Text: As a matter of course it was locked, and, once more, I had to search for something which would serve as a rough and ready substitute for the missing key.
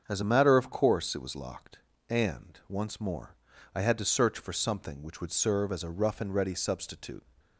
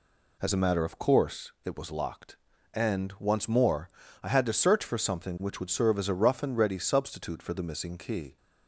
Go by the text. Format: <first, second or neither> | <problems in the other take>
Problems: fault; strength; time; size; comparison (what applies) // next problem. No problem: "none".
second | starts louder than the rest; until 1.0 s; 7 dB // stops before "for the missing key"; at 7.3 s